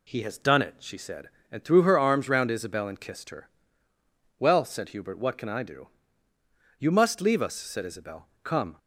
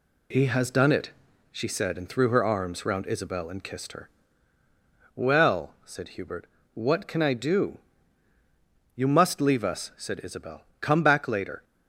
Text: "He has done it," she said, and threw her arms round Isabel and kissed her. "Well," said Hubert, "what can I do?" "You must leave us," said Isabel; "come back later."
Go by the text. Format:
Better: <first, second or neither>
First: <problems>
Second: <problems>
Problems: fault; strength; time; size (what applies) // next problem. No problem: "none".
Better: second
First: stops before "back later"; at 8.7 s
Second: none